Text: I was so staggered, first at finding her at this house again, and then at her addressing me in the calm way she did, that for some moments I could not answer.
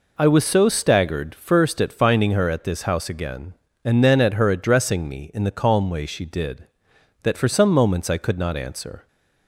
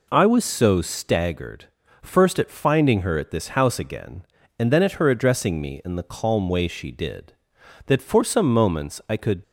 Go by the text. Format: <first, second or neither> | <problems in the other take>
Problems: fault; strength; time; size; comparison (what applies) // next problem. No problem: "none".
first | stops before "not answer"; at 9.4 s